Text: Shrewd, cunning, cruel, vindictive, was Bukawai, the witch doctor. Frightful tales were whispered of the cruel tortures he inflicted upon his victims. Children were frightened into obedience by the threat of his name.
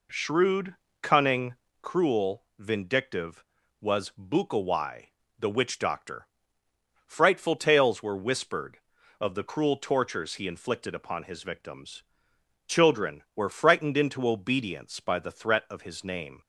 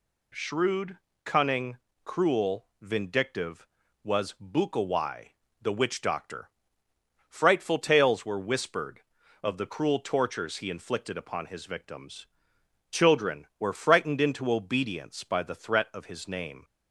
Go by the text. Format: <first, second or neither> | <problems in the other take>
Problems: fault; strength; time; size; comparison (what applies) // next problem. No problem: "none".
second | starts louder than the rest; slight; until 1.9 s; 3.5 dB